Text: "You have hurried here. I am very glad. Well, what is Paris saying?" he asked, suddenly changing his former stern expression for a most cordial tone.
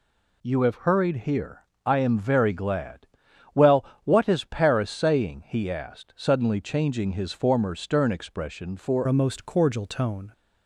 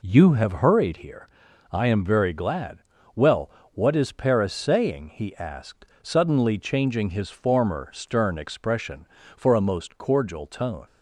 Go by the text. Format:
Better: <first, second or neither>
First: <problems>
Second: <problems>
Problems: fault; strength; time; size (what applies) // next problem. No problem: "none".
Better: second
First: changes voice at "a"; from 9.0 s on; 1.3 s long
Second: none